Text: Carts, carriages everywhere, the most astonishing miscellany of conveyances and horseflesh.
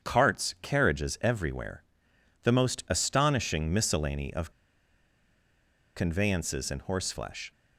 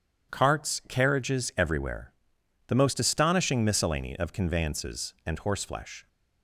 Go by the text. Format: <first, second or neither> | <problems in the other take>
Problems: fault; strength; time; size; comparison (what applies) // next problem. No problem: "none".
second | starts louder than the rest; strong; until 1.1 s; 7.5 dB // pauses between "of" and "conveyances"; strong; at 4.4 s; 1.4 s long